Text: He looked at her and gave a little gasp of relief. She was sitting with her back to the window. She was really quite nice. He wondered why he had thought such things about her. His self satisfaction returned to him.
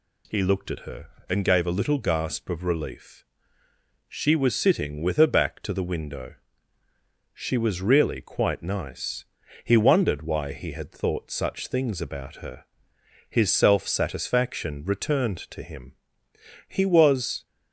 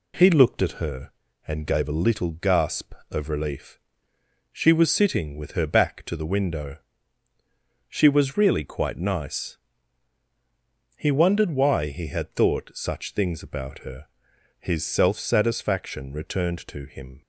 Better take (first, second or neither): second